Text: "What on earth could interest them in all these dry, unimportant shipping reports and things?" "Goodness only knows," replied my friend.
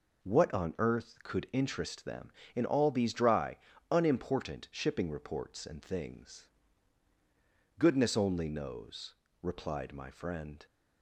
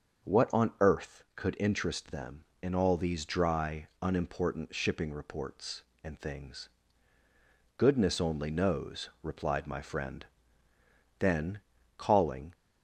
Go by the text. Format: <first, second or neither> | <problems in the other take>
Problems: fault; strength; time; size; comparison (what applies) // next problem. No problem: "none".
first | starts louder than the rest; until 1.5 s; 6.5 dB // goes on to say "Then calling"; from 11.1 s on; 1.3 s long